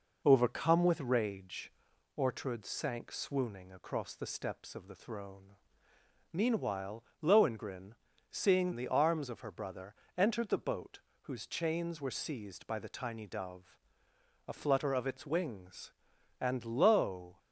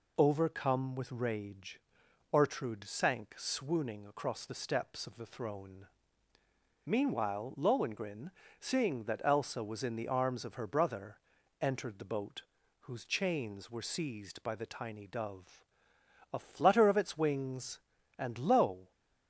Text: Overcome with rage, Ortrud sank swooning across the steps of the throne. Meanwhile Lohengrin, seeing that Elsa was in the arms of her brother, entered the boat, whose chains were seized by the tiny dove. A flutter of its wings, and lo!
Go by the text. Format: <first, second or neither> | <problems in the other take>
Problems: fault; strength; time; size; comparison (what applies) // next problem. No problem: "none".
second | pauses between "Meanwhile" and "Lohengrin"; slight; at 7.0 s; 0.18 s long // skips "that Elsa was in"; at 8.7 s